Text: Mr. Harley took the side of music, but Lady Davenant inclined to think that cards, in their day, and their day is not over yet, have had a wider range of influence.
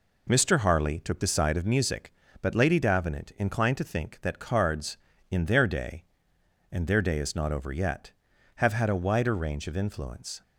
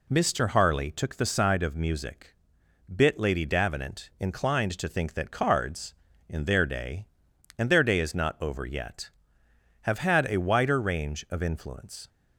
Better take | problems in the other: first | says "bit" for "but"; at 2.9 s

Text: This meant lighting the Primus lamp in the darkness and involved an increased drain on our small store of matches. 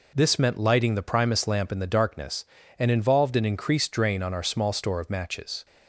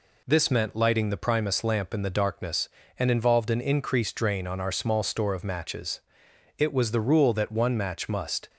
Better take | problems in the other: first | goes on to say "It was the rule that one match must"; strong; from 6.5 s on; 1.9 s long

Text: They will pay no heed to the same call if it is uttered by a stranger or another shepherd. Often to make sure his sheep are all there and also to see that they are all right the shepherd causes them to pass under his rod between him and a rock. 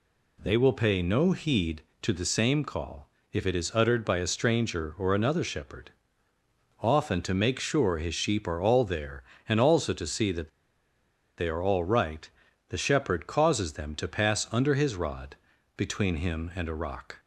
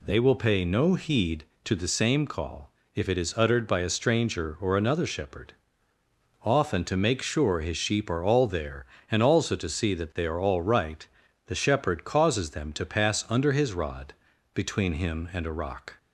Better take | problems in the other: second | pauses between "call" and "if"; slight; at 3.0 s; 0.24 s long; slight in the second // pauses between "that" and "they"; noticeable; at 10.4 s; 0.88 s long // pauses between "right" and "the"; at 12.2 s; 0.40 s long; also in the second // pauses between "rod" and "between"; at 15.3 s; 0.40 s long; also in the second

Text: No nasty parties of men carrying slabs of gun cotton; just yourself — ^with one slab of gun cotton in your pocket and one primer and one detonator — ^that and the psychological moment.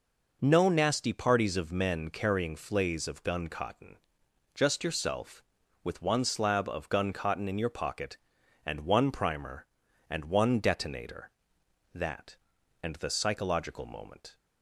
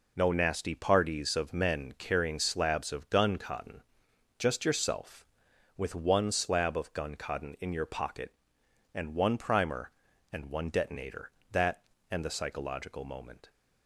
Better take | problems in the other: second | says "flays" for "slabs"; at 2.5 s

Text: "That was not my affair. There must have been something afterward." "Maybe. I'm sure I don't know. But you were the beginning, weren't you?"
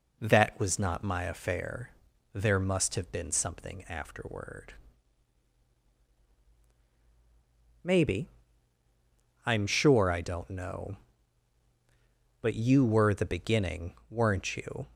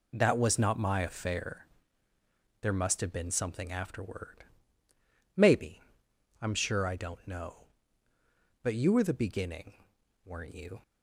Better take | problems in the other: neither | none

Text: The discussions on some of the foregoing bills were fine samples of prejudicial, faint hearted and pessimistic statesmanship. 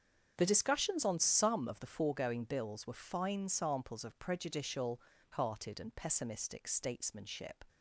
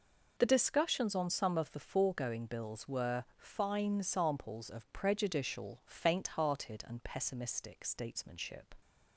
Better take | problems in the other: second | starts louder than the rest; strong; until 1.3 s; 7.5 dB // skips "faint"; at 5.1 s

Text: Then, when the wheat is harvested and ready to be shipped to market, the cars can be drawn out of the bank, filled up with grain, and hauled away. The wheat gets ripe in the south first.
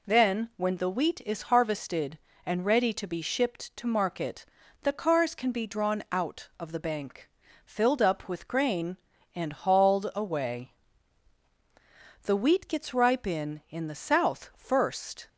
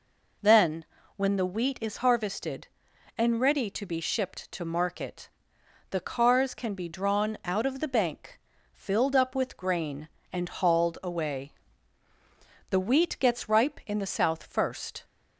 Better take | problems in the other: second | says "in" twice; at 13.6 s

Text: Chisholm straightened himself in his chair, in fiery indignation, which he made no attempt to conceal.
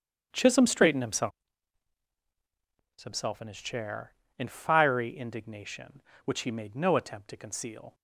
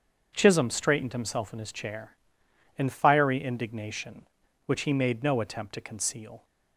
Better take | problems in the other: second | starts louder than the rest; strong; until 1.3 s; 9 dB; also in the second // says "himself" twice; at 3.0 s

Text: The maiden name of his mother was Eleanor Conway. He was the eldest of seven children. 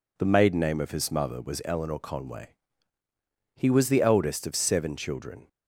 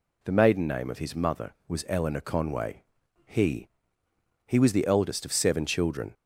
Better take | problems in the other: first | says "He" twice; at 4.4 s

